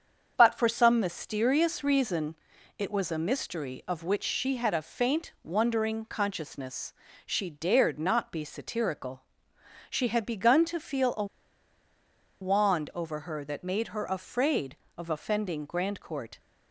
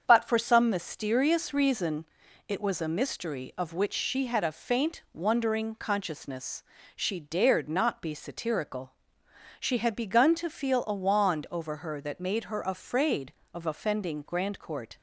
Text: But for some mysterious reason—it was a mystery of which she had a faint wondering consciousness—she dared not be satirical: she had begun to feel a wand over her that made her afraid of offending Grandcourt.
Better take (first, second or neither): second